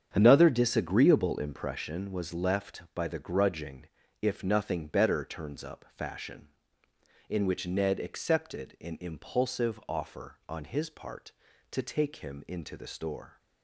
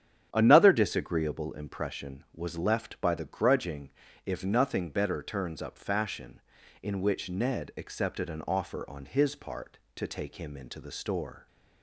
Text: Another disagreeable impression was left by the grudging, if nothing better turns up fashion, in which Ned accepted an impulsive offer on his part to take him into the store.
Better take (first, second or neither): first